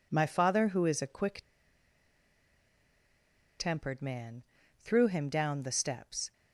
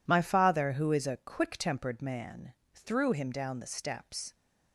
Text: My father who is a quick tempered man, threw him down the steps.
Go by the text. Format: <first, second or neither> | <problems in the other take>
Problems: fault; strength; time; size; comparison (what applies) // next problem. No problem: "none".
second | pauses between "quick" and "tempered"; strong; at 1.4 s; 2.1 s long